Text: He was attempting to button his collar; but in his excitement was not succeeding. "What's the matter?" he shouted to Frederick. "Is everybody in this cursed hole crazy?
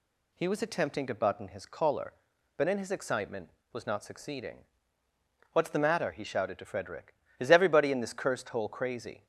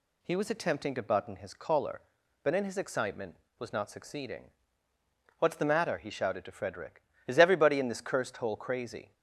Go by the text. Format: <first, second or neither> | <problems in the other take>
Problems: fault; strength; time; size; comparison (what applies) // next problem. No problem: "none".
neither | none